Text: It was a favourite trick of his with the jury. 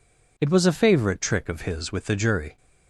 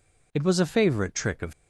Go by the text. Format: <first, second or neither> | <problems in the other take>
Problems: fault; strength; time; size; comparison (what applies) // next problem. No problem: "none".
first | stops before "his with the jury"; at 1.5 s